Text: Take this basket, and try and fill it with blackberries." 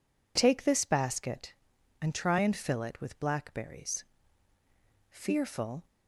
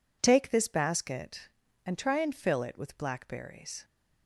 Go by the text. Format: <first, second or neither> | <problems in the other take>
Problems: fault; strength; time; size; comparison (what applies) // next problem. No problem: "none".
second | goes on to say "Fearful"; noticeable; from 5.0 s on; 0.76 s long